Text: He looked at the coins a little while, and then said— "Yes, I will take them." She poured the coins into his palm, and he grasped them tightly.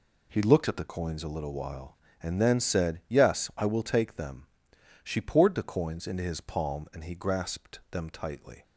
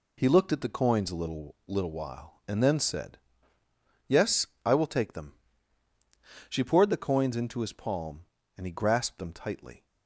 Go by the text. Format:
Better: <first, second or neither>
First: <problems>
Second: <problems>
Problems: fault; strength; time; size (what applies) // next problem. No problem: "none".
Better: first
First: none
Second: says "little" twice; at 1.6 s